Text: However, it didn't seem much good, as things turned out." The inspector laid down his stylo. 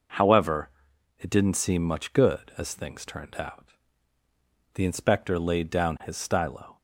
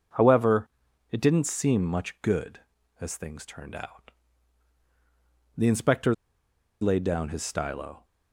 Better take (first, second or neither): first